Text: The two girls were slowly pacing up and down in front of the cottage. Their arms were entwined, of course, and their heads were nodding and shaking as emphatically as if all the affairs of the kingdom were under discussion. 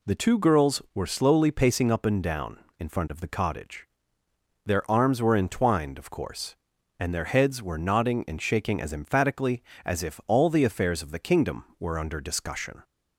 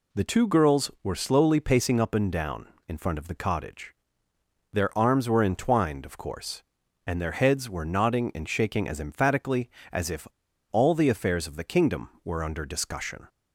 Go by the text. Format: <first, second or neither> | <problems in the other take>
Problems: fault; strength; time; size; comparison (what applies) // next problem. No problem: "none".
first | pauses between "if" and "all"; at 10.2 s; 0.45 s long